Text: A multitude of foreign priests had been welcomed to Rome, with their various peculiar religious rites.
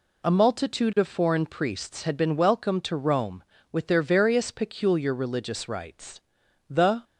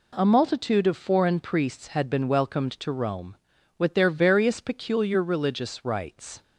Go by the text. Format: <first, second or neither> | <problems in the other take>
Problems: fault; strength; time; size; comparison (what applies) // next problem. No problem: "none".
second | goes on to say "The"; slight; from 6.6 s on; 0.34 s long